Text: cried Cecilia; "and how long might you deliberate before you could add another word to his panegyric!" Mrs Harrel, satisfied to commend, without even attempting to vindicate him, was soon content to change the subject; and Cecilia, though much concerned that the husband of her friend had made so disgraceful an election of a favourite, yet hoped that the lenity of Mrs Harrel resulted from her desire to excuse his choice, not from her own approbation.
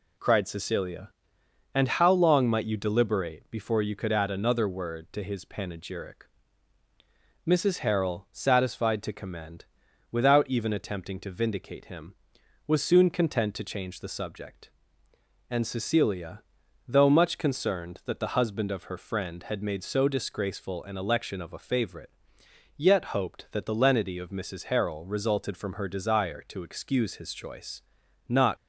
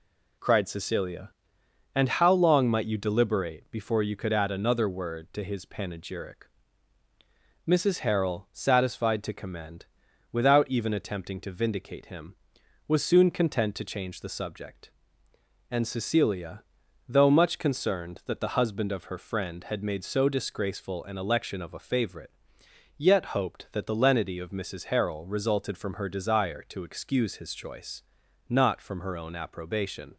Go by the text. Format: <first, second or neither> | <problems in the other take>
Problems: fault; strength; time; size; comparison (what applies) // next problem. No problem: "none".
second | stops before "from her own approbation"; at 28.5 s